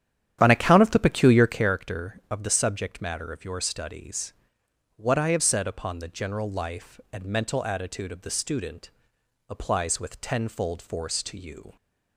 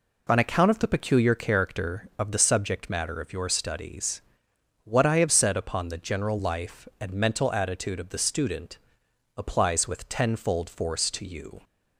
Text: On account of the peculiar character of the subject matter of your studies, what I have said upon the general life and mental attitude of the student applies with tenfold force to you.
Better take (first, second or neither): second